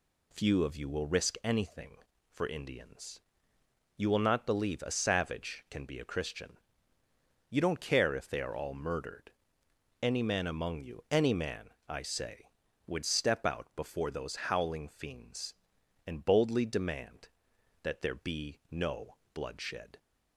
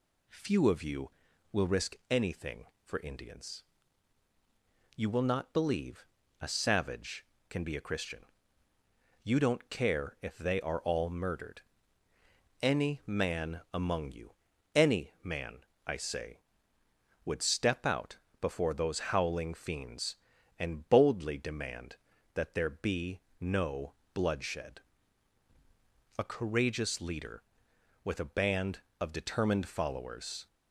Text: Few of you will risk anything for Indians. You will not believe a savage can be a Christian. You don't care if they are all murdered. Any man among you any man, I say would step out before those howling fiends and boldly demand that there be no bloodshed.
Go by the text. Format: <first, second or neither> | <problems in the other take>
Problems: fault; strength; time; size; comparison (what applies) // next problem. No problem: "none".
first | pauses between "believe" and "a"; slight; at 6.0 s; 0.36 s long // pauses between "you" and "any"; at 14.3 s; 0.42 s long // pauses between "out" and "before"; slight; at 18.1 s; 0.22 s long // pauses between "be" and "no"; slight; at 23.2 s; 0.20 s long // pauses between "no" and "bloodshed"; slight; at 23.9 s; 0.20 s long; slight in the first // goes on to say "A courageous leader with a band of determined followers"; strong; from 26.1 s on; 4.3 s long